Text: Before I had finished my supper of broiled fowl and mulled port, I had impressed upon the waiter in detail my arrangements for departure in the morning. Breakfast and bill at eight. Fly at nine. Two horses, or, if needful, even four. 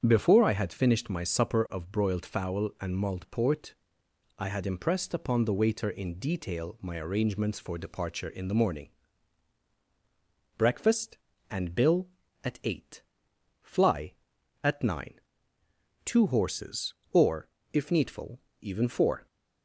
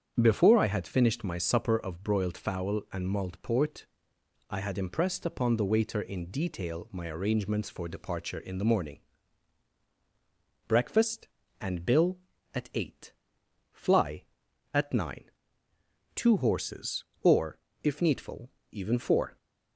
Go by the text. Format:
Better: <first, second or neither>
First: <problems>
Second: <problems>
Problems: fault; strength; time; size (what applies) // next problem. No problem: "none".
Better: neither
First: starts louder than the rest; strong; until 1.0 s; 8 dB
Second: starts louder than the rest; strong; until 1.2 s; 8 dB